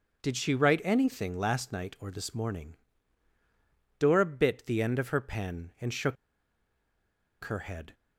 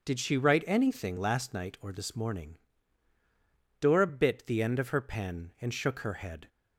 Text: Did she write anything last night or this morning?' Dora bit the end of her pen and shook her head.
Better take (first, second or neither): second